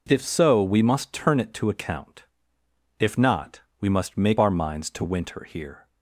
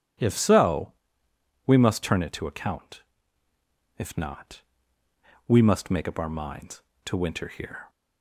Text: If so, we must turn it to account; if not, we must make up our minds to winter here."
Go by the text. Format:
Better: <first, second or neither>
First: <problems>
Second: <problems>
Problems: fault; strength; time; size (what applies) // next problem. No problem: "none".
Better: second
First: skips "up"; at 4.3 s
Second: none